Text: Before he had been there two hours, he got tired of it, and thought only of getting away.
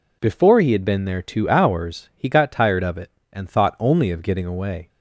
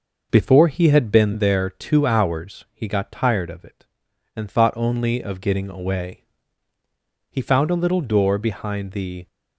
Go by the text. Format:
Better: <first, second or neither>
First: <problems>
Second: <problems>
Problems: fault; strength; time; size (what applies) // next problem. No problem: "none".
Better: first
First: none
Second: goes on to say "He found a little door behind the"; strong; from 7.2 s on; 1.9 s long